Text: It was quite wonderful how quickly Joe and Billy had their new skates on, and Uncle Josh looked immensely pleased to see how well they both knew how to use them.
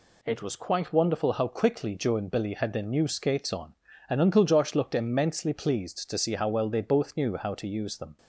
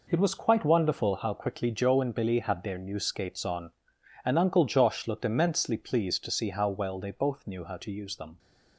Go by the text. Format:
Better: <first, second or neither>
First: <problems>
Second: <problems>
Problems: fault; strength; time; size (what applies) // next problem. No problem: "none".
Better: neither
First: none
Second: none